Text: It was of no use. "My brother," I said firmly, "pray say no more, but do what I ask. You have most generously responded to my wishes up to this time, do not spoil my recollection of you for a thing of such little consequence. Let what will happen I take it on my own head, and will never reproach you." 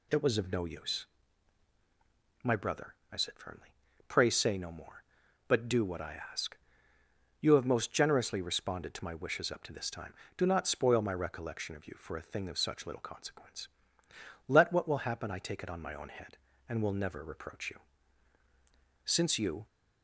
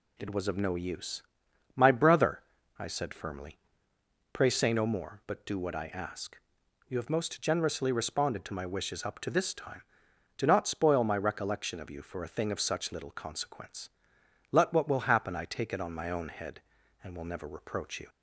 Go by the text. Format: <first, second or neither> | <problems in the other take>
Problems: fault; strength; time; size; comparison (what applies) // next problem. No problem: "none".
second | goes on to say "Since you"; noticeable; from 19.0 s on; 0.62 s long